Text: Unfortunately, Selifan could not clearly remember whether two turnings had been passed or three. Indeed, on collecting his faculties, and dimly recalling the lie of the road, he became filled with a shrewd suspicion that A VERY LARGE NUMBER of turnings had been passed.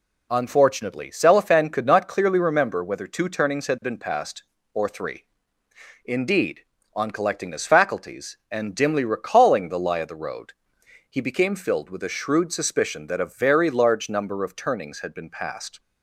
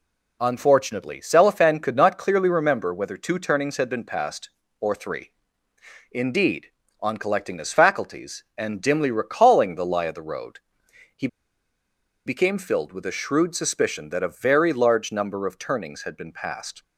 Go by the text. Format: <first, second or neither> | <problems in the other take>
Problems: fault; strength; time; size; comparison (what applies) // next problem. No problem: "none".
first | pauses between "he" and "became"; at 11.2 s; 0.99 s long